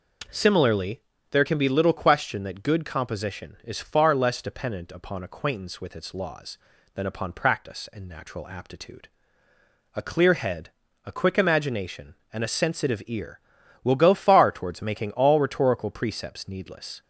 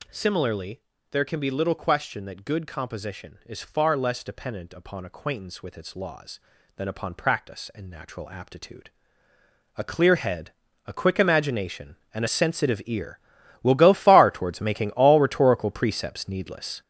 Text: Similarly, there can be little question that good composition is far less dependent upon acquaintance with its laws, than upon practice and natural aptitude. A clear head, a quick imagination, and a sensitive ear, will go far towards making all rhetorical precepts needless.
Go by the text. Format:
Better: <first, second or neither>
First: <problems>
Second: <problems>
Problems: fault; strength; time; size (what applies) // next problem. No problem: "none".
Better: first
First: none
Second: gets louder; strong; throughout; 7.5 dB